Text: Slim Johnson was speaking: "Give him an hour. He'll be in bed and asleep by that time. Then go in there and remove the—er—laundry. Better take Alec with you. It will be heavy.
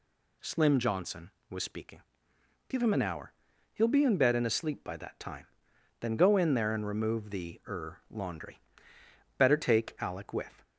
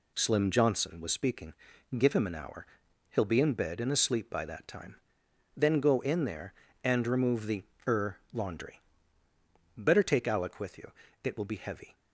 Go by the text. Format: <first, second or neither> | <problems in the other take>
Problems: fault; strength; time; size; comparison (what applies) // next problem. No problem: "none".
second | stops before "you It will be heavy"; at 10.6 s